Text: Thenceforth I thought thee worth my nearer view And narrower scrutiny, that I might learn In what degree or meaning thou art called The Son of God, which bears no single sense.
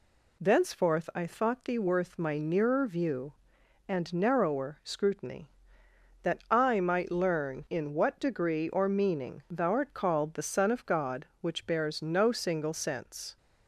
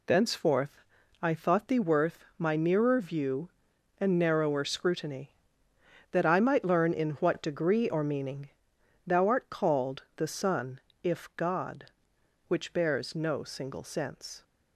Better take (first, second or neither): first